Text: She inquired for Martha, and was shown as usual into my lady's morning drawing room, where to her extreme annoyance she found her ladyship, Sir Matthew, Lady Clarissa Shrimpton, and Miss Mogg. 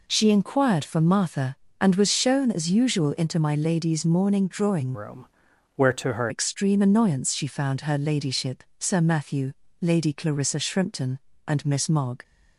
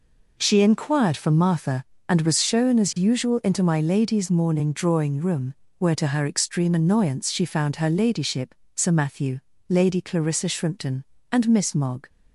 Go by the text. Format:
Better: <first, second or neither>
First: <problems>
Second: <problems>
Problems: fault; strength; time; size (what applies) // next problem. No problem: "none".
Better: second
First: changes voice from "room" to "her"; from 4.9 to 6.2 s; 1.3 s long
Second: none